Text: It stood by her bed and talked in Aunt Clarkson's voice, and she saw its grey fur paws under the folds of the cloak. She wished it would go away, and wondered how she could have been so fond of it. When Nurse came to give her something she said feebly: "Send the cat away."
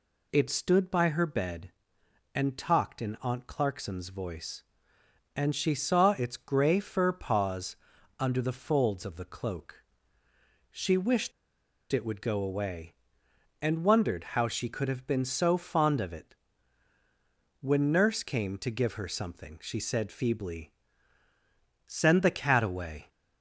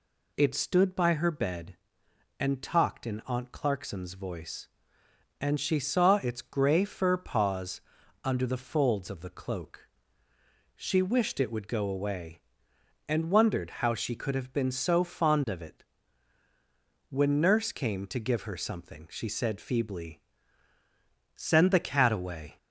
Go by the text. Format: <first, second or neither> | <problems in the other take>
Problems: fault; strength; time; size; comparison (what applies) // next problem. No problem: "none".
second | pauses between "paws" and "under"; at 7.7 s; 0.44 s long; also in the second // pauses between "wished" and "it"; noticeable; at 11.3 s; 0.60 s long